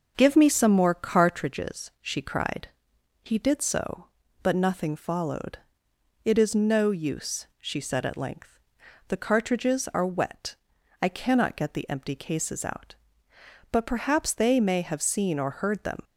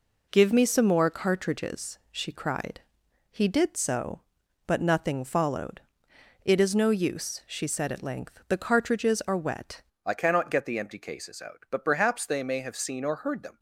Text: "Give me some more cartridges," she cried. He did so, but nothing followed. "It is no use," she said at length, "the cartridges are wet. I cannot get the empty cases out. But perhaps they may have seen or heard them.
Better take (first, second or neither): first